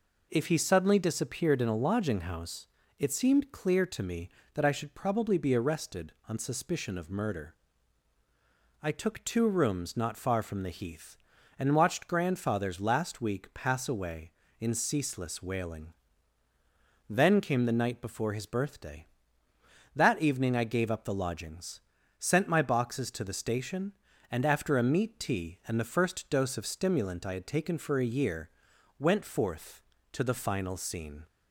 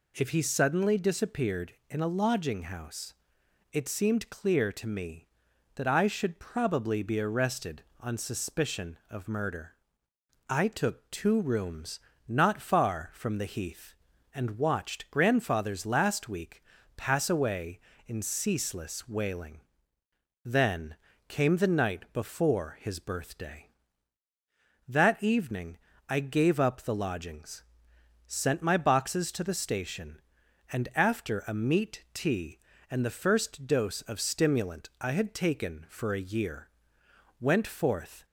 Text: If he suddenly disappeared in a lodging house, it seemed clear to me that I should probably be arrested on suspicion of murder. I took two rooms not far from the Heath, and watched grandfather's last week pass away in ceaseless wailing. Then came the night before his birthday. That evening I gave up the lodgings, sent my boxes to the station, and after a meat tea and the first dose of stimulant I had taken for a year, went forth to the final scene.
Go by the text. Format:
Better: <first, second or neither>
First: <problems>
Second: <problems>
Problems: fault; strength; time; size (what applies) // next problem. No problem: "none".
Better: first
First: none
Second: pauses between "rooms" and "not"; slight; at 11.9 s; 0.30 s long // pauses between "week" and "pass"; slight; at 16.6 s; 0.32 s long // pauses between "Then" and "came"; slight; at 20.9 s; 0.32 s long // pauses between "evening" and "I"; slight; at 25.7 s; 0.30 s long // stops before "to the final scene"; at 38.2 s